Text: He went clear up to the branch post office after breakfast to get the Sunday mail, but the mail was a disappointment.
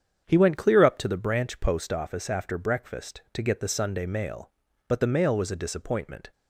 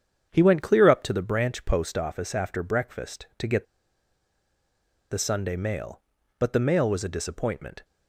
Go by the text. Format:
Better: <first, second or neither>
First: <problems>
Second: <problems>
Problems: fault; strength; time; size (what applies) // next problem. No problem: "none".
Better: first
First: starts louder than the rest; strong; until 1.2 s; 8 dB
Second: starts louder than the rest; strong; until 1.3 s; 8 dB // pauses between "get" and "the"; strong; at 3.6 s; 1.4 s long